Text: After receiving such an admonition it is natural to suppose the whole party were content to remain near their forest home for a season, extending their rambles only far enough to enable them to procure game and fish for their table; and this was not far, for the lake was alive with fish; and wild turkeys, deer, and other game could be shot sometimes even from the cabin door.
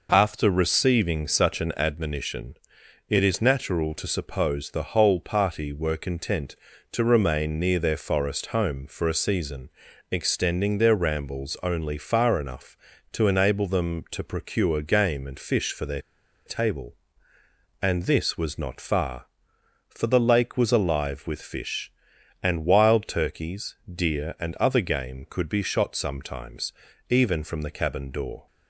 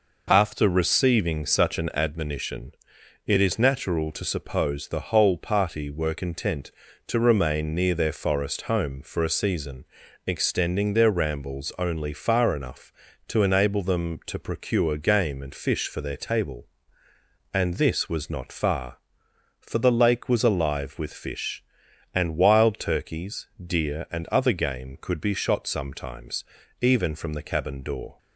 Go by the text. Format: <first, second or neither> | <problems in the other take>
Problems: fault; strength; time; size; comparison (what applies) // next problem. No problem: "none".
second | pauses between "admonition" and "it"; noticeable; at 2.5 s; 0.54 s long; noticeable in the second // pauses between "their" and "table"; at 16.0 s; 0.45 s long // pauses between "sometimes" and "even"; at 26.7 s; 0.38 s long; also in the second